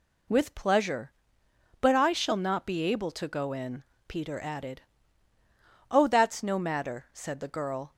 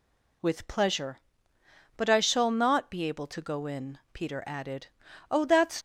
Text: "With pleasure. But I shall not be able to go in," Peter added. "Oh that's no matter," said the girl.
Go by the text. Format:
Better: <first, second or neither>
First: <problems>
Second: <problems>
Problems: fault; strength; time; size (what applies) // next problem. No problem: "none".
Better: first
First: none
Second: stops before "no matter said the girl"; at 5.7 s